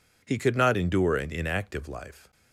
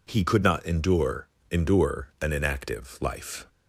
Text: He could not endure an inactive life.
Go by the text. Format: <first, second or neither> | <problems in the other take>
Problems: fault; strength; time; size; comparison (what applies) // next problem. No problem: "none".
first | says "endure" twice; at 1.5 s